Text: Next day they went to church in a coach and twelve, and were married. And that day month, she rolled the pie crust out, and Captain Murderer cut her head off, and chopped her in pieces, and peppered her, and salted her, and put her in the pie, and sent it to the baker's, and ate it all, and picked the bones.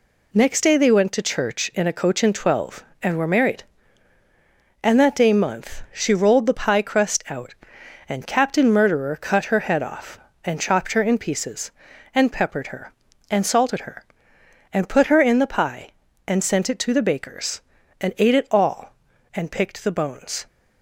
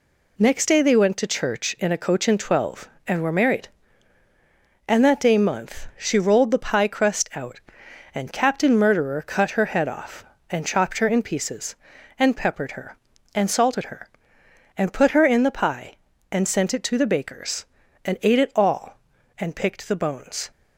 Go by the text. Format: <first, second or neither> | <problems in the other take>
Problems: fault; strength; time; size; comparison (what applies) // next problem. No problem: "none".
neither | none